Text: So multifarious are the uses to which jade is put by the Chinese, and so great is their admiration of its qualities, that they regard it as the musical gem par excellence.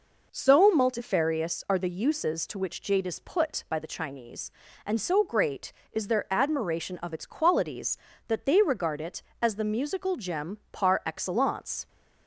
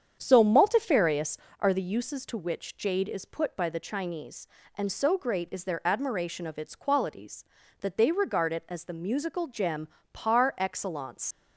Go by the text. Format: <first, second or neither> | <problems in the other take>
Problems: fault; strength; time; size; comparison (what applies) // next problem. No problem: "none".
first | starts louder than the rest; strong; until 1.2 s; 8 dB // pauses between "gem" and "par"; slight; at 9.8 s; 0.24 s long // leaves "excellence" unfinished; at 11.3 s; 85 ms